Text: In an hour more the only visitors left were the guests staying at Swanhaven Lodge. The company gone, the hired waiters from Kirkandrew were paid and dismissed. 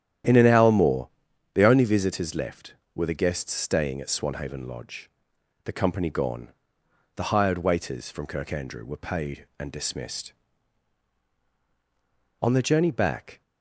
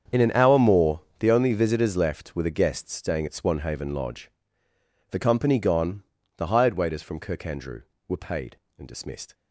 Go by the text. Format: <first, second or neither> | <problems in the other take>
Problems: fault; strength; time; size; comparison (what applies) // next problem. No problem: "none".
second | starts louder than the rest; strong; until 1.7 s; 10.5 dB; strong in the second // pauses between "more" and "the"; at 1.0 s; 0.44 s long; slight in the second // goes on to say "On the journey back"; noticeable; from 12.3 s on; 1.0 s long